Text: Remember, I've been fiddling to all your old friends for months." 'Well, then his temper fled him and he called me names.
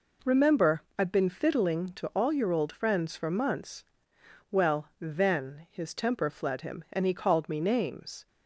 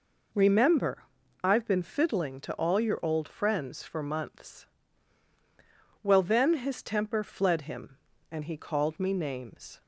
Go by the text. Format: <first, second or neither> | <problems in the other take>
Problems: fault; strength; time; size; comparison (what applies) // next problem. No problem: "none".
neither | none